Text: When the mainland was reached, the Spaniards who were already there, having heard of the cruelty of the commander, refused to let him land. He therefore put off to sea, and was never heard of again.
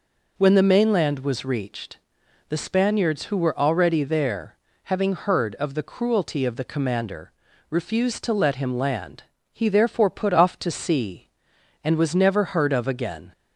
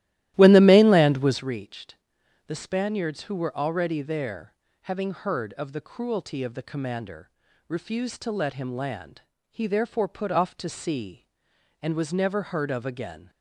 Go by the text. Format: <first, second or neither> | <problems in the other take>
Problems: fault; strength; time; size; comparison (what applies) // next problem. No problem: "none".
first | starts louder than the rest; strong; until 1.5 s; 14.5 dB